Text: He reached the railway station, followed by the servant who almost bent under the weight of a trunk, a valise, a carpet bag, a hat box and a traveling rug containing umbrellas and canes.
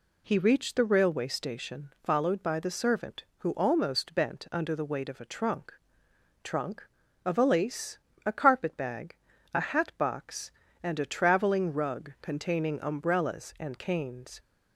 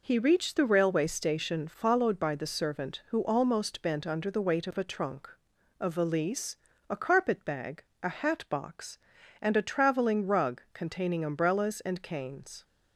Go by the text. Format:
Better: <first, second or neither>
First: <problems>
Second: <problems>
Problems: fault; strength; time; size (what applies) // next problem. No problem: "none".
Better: second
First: says "trunk" twice; at 6.4 s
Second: none